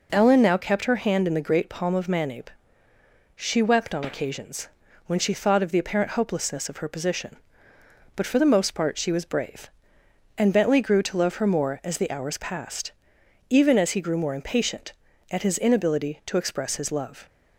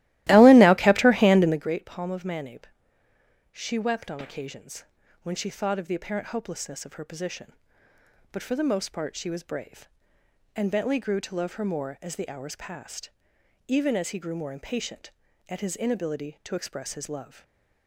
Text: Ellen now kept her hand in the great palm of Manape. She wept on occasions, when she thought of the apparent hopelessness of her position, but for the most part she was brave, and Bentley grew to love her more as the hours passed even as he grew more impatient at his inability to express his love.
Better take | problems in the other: first | starts louder than the rest; strong; until 1.7 s; 16.5 dB // pauses between "passed" and "even"; noticeable; at 13.0 s; 0.60 s long; noticeable in the first // stays silent after the last word; slight; from 17.2 s on; 0.6 s long

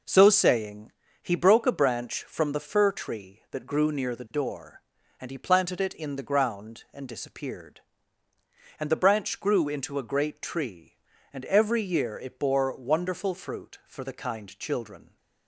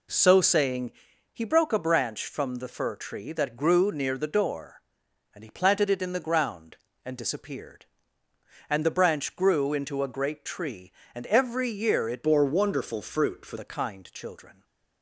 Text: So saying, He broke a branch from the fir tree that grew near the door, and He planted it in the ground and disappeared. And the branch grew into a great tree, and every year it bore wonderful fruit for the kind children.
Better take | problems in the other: first | changes voice from "bore" to "for"; from 12.2 to 13.5 s; 1.3 s long

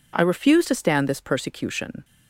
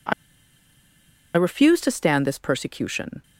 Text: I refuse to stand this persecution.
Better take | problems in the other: first | pauses between "I" and "refuse"; at 0.1 s; 1.2 s long

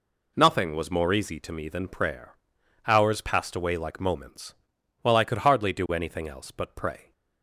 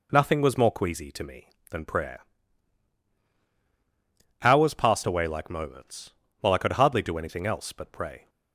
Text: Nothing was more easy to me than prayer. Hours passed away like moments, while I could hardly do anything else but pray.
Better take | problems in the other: first | says "queasy" for "easy"; at 0.7 s

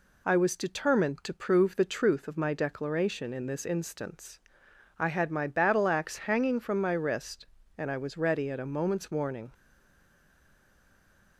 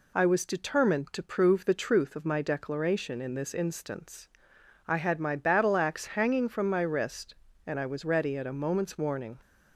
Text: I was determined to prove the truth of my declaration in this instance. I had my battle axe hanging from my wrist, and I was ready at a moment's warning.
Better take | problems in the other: second | stays silent after the last word; noticeable; from 9.5 s on; 1.8 s long

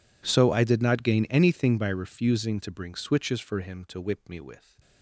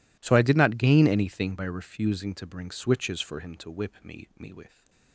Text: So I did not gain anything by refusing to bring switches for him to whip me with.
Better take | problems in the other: first | says "me" twice; at 4.3 s

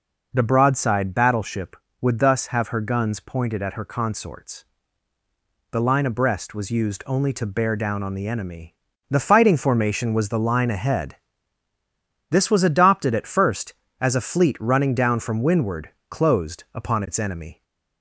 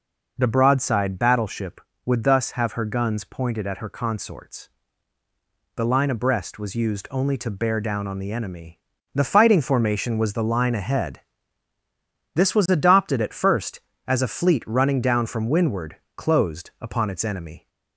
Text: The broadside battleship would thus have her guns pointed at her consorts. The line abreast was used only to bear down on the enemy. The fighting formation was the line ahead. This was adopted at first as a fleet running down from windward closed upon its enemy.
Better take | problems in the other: neither | pauses between "windward" and "closed"; slight; the same in both

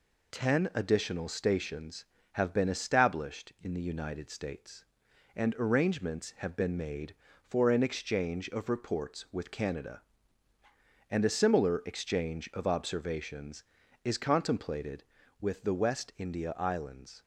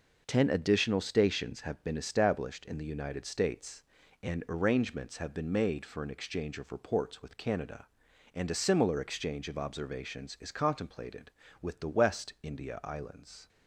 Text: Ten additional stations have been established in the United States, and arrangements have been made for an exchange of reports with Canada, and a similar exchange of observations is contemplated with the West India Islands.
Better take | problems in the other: neither | none

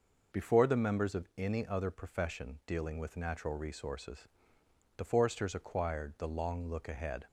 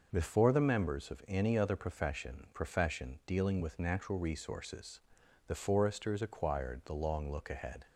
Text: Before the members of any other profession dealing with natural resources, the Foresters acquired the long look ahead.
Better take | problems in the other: first | says "profession" twice; at 2.5 s

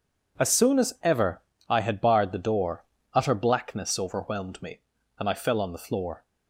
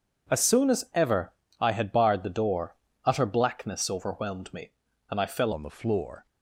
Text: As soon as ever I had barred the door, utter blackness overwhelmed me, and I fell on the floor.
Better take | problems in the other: first | pauses between "ever" and "I"; slight; at 1.3 s; 0.26 s long; slight in the first // changes voice at "on"; from 5.5 s on; 0.7 s long

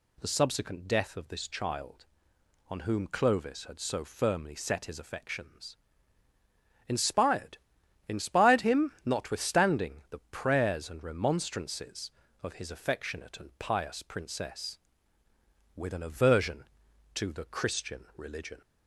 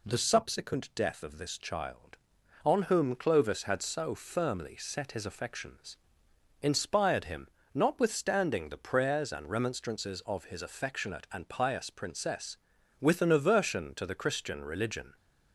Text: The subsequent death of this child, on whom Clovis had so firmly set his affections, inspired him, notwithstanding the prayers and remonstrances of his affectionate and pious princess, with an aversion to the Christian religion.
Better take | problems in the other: second | says "inspired" twice; at 8.0 s

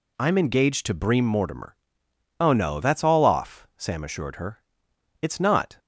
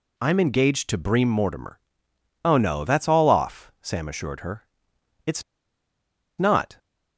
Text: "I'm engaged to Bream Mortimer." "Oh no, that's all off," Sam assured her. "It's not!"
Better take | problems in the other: first | pauses between "It's" and "not"; noticeable; at 5.4 s; 0.96 s long

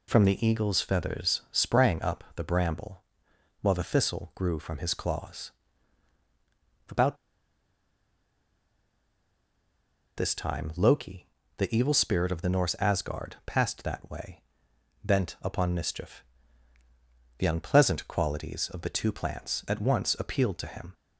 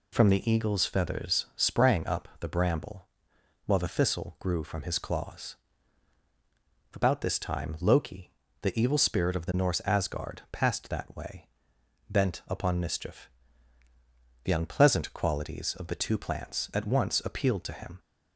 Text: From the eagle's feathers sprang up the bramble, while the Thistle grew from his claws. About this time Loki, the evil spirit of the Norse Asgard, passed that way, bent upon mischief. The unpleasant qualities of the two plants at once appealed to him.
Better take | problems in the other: second | pauses between "About" and "this"; strong; at 7.1 s; 3.0 s long

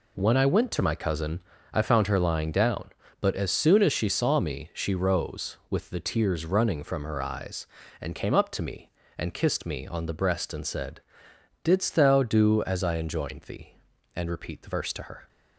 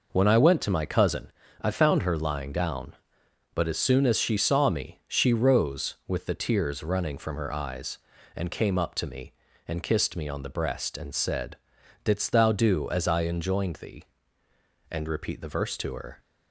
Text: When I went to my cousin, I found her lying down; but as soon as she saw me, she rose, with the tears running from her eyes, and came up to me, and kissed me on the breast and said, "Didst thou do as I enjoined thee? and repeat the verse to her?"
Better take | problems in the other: neither | none

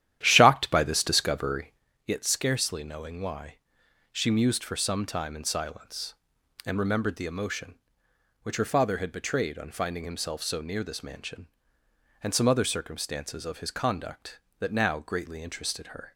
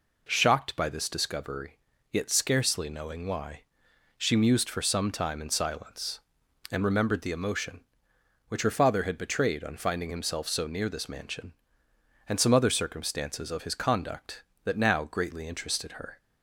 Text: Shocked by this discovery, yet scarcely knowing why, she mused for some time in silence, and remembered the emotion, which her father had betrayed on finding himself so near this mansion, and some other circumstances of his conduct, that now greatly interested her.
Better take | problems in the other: second | starts louder than the rest; strong; until 1.9 s; 11.5 dB

